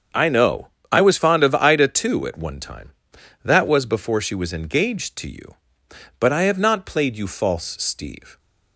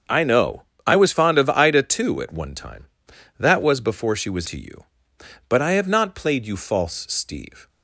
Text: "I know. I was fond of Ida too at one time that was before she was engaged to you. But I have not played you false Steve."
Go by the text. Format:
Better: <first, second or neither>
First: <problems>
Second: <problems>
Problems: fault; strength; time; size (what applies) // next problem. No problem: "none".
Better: first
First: starts louder than the rest; until 1.3 s; 7 dB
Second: starts louder than the rest; until 1.3 s; 7 dB // skips "engaged"; at 4.4 s